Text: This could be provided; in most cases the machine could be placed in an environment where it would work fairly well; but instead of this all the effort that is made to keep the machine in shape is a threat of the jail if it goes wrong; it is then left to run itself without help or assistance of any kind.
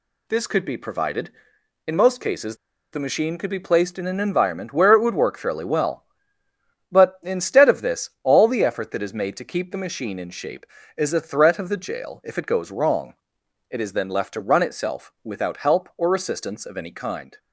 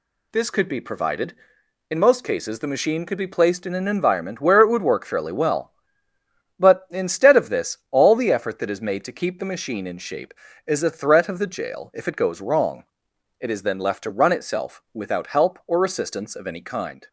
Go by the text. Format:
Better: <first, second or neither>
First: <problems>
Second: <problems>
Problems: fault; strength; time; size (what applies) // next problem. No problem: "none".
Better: second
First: pauses between "cases" and "the"; at 2.5 s; 0.37 s long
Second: none